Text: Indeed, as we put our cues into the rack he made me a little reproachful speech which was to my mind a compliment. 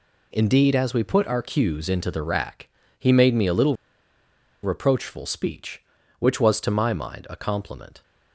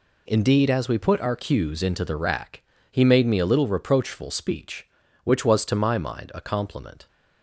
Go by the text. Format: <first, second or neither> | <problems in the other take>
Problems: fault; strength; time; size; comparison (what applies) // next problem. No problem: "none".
second | pauses between "rack" and "he"; slight; at 2.6 s; 0.32 s long; slight in the second // pauses between "little" and "reproachful"; noticeable; at 3.7 s; 0.88 s long